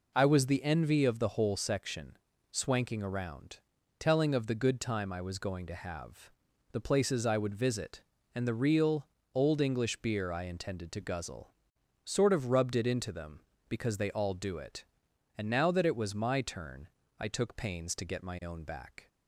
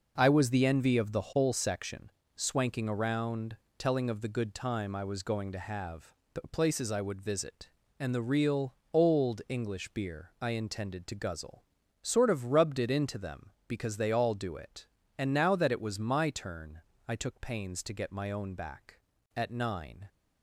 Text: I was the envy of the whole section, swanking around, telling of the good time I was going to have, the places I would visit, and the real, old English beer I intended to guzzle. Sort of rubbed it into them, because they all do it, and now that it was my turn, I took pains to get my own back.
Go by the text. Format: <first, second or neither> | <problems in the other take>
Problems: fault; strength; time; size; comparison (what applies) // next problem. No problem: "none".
first | goes on to say "At nine"; noticeable; from 19.3 s on; 0.72 s long